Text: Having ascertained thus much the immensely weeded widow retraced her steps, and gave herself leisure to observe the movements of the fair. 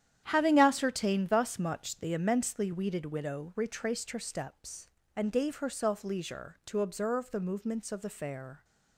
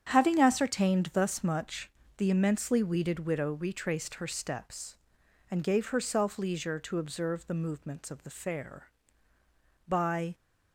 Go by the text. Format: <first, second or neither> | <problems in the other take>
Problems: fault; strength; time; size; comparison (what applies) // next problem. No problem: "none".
first | starts louder than the rest; strong; until 1.1 s; 8.5 dB; strong in the first // pauses between "much" and "the"; slight; at 1.8 s; 0.26 s long // goes on to say "By"; slight; from 9.8 s on; 0.46 s long